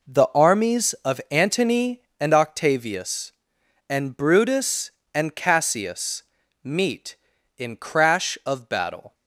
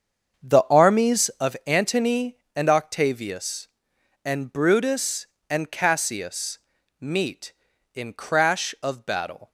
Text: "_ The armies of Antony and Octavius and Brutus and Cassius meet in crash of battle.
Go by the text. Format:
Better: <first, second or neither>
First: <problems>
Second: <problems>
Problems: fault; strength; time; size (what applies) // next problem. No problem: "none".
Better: first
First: pauses between "Cassius" and "meet"; at 6.2 s; 0.40 s long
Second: starts louder than the rest; until 1.5 s; 7 dB // pauses between "Cassius" and "meet"; at 6.5 s; 0.42 s long